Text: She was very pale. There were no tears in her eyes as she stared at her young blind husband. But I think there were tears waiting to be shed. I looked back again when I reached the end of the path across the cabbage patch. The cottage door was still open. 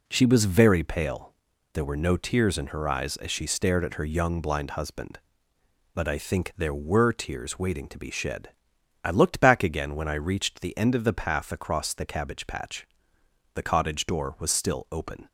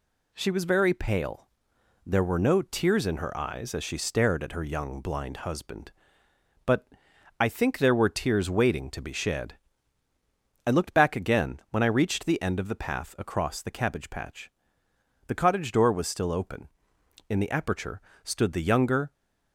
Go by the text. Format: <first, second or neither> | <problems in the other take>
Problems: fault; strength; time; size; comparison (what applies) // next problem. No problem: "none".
first | pauses between "But" and "I"; noticeable; at 6.8 s; 0.52 s long // goes on to say "In the aperture stood the younger"; strong; from 17.2 s on; 1.8 s long